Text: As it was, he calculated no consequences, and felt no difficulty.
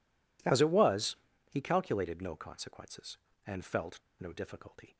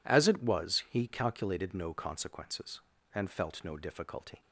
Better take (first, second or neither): second